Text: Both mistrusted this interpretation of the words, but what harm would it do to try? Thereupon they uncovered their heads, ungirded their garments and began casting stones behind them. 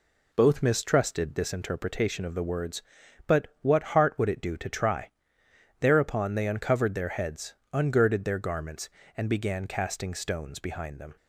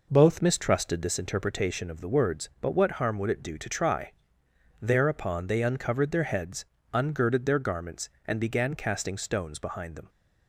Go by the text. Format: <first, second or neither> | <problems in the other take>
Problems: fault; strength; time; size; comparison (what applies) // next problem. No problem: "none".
second | says "heart" for "harm"; at 3.9 s